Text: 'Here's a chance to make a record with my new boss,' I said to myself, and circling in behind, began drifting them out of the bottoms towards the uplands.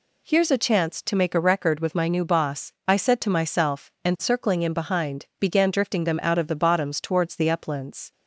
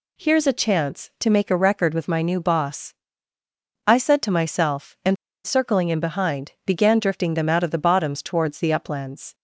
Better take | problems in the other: first | pauses between "and" and "circling"; slight; at 5.1 s; 0.30 s long

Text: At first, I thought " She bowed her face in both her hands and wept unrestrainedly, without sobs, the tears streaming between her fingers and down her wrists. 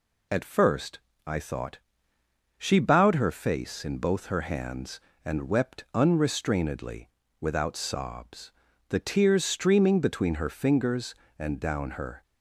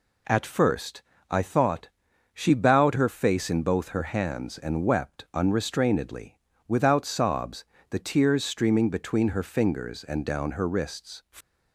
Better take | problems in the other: second | stops before "wrists"; at 12.2 s

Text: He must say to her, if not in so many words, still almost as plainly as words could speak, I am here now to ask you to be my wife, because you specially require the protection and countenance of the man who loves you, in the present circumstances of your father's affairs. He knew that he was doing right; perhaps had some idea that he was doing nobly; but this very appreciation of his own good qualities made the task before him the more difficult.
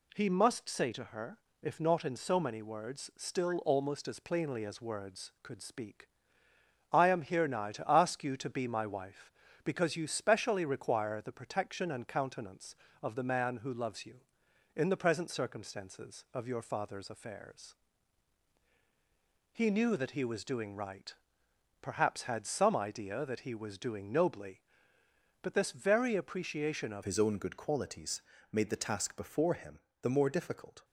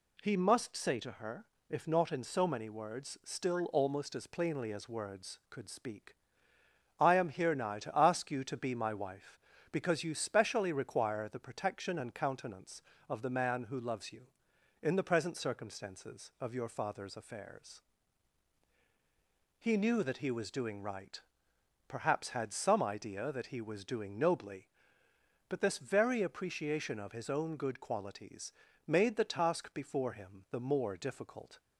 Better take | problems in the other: second | changes voice at "his"; from 27.0 s on; 3.8 s long // pauses between "qualities" and "made"; slight; at 28.2 s; 0.28 s long; slight in the second // pauses between "him" and "the"; slight; at 29.7 s; 0.22 s long

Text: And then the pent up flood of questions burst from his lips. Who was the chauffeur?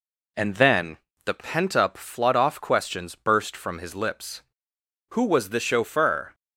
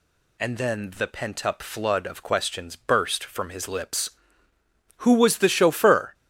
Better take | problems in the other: second | pauses between "then" and "the"; slight; at 0.9 s; 0.28 s long // says "off" for "of"; at 2.3 s

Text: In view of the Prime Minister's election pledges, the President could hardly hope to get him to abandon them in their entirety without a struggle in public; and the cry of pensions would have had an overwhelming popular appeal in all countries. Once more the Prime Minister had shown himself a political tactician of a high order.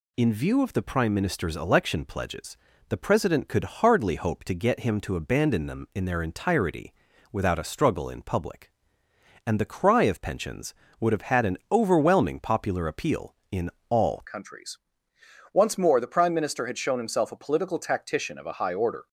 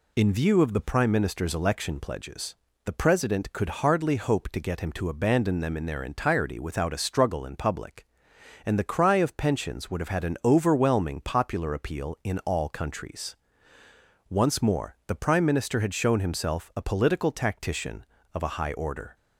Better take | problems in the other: second | pauses between "entirety" and "without"; at 6.9 s; 0.40 s long // pauses between "in" and "all"; slight; at 13.6 s; 0.20 s long // changes voice at "countries"; from 14.2 s on; 4.8 s long

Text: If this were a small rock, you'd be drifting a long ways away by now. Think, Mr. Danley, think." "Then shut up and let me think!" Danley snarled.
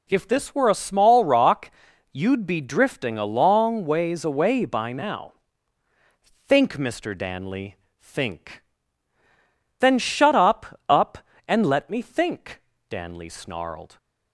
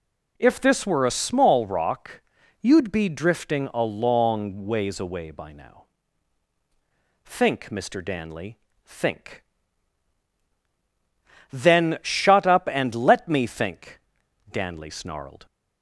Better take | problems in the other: second | says "up" twice; at 10.8 s

